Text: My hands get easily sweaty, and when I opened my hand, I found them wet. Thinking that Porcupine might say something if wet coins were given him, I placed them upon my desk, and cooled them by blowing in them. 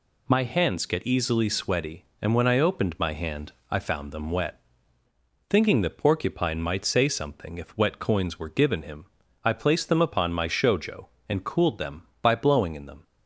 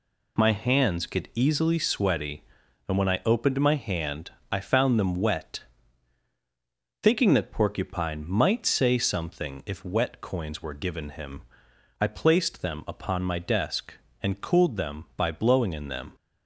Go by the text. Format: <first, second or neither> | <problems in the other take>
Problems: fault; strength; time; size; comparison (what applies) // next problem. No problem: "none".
second | says "shojo" for "desk"; at 10.4 s